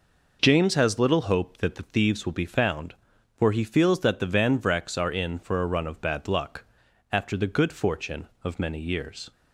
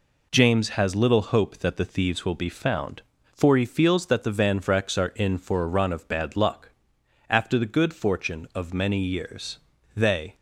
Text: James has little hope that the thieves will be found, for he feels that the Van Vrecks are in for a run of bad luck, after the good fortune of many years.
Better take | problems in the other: first | goes on to say "They"; slight; from 9.9 s on; 0.40 s long

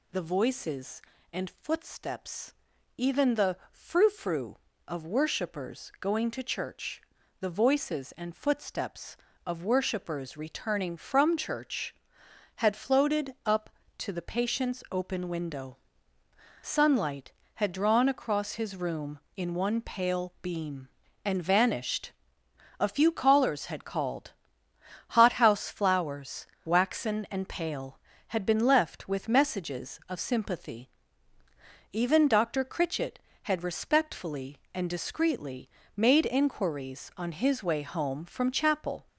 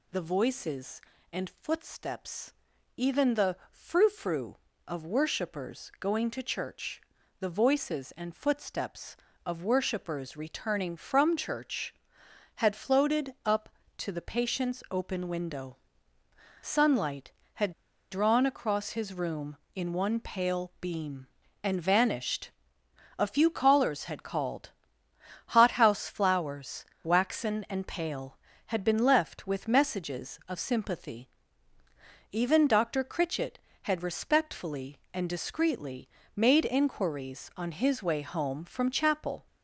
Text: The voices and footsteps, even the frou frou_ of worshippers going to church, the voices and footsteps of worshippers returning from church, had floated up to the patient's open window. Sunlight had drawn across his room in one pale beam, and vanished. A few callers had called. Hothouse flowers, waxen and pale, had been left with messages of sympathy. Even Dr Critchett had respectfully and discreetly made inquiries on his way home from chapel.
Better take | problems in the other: first | pauses between "had" and "drawn"; at 17.7 s; 0.40 s long // pauses between "discreetly" and "made"; slight; at 36.0 s; 0.26 s long; slight in the first

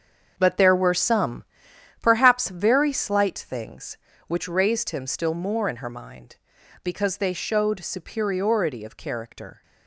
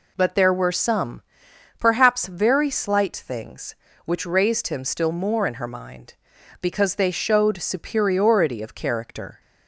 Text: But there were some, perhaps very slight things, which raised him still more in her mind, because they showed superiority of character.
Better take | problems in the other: second | gets quieter; strong; throughout; 10 dB

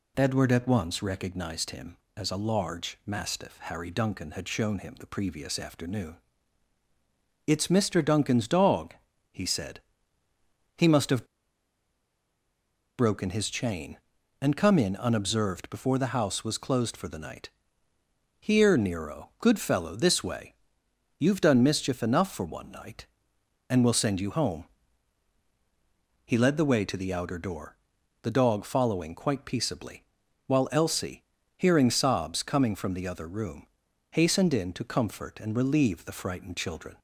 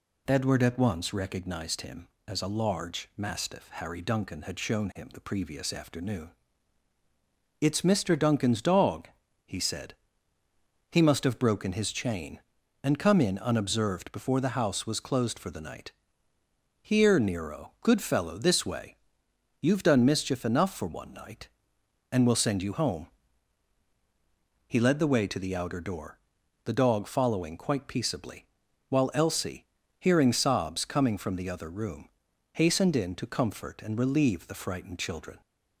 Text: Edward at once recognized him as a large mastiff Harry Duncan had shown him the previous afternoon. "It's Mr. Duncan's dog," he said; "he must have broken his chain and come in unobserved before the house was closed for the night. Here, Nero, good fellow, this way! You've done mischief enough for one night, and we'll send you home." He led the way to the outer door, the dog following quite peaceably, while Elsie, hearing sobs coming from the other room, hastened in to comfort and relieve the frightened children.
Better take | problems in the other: second | pauses between "have" and "broken"; strong; at 11.2 s; 1.7 s long

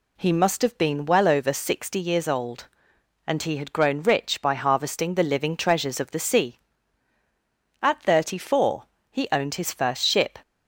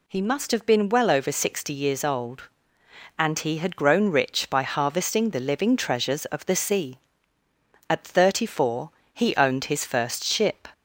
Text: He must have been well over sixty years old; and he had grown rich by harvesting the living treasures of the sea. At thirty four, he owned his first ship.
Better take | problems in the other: neither | none

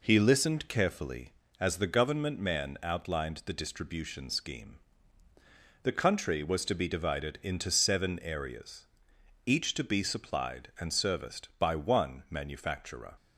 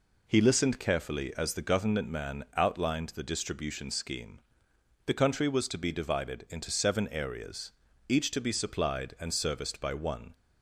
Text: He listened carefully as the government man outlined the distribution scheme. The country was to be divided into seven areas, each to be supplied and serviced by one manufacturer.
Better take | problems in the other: first | stops before "manufacturer"; at 10.3 s

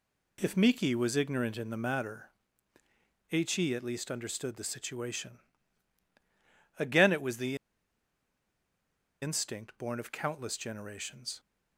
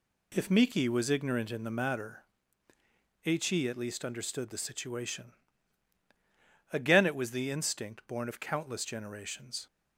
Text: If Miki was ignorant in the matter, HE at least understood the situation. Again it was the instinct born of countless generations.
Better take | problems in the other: second | pauses between "the" and "instinct"; strong; at 7.5 s; 1.6 s long

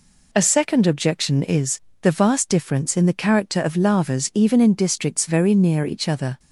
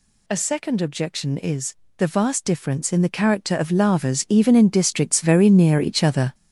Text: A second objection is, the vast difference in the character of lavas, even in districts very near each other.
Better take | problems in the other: first | gets louder; strong; throughout; 8 dB

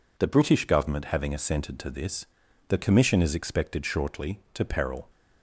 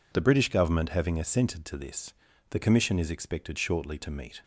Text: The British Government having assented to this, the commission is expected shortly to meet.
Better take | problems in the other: second | says "peril" for "meet"; at 4.6 s

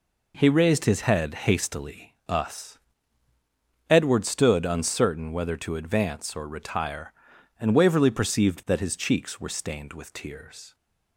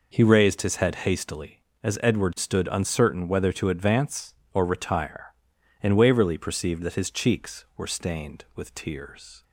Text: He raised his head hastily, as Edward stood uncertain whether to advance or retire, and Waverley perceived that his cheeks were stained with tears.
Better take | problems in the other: second | says "us" for "as"; at 2.2 s

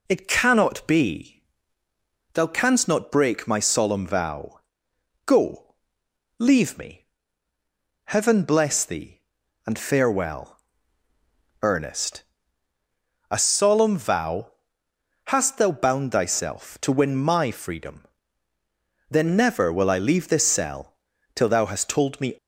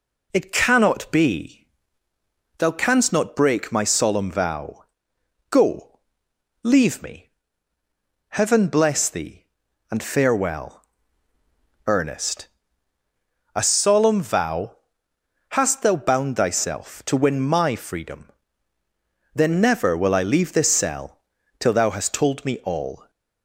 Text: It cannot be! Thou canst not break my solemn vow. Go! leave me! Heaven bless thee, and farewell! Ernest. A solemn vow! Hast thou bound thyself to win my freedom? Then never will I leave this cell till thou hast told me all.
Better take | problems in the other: second | pauses between "cell" and "till"; at 20.9 s; 0.40 s long; also in the second // stops before "all"; at 22.3 s

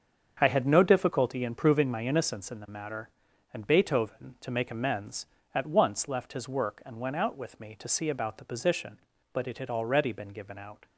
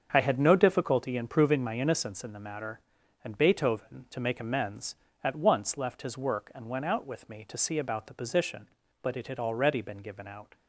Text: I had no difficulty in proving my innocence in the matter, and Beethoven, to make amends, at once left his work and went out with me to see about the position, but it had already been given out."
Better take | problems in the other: neither | starts louder than the rest; strong; the same in both

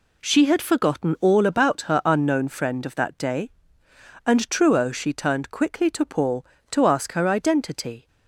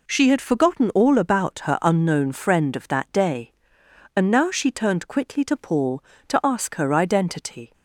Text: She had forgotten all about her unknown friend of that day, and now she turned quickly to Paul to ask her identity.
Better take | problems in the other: second | says "truo" for "now"; at 4.5 s

